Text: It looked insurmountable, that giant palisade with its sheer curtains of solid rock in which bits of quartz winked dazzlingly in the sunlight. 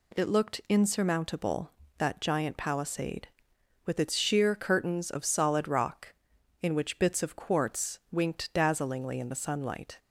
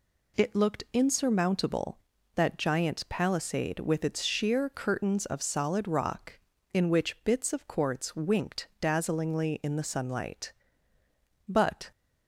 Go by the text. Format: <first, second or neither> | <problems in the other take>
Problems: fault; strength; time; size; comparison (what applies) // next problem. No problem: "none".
first | goes on to say "But"; slight; from 11.4 s on; 0.44 s long